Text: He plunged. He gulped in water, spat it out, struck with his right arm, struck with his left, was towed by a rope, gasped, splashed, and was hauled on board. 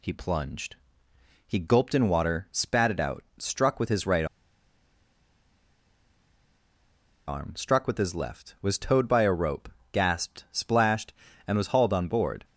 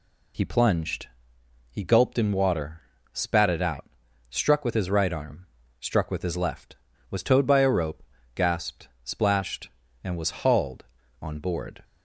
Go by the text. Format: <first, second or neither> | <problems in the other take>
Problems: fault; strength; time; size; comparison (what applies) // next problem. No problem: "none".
second | pauses between "right" and "arm"; strong; at 4.2 s; 3.0 s long